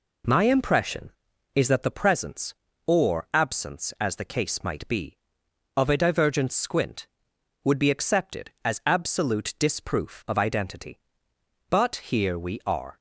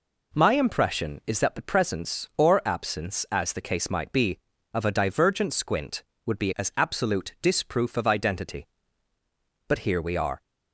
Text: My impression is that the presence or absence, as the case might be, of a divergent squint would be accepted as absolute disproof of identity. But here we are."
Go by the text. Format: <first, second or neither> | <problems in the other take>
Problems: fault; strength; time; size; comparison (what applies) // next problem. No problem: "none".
first | skips "accepted"; at 6.5 s